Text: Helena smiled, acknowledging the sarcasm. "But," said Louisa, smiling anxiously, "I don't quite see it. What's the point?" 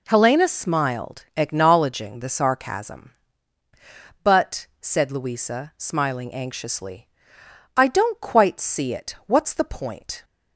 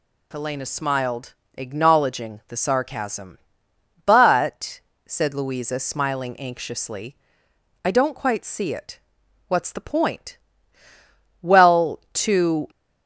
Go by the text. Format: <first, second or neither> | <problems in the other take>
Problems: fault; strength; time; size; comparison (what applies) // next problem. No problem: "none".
first | goes on to say "Well to"; noticeable; from 11.4 s on; 1.2 s long